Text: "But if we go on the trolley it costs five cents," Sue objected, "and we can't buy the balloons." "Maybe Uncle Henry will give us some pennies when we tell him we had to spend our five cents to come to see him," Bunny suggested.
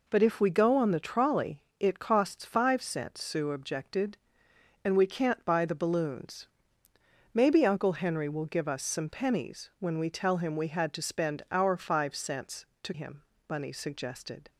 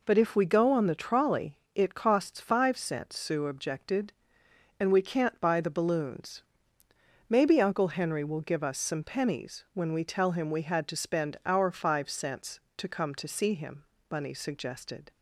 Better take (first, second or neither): second